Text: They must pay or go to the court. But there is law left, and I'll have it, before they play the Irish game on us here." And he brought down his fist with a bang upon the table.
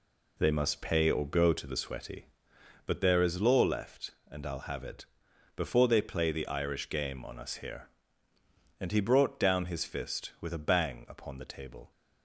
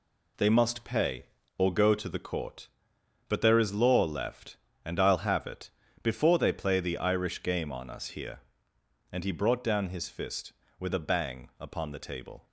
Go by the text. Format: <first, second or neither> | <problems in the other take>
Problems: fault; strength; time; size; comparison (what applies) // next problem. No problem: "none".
second | says "sweaty" for "court"; at 1.7 s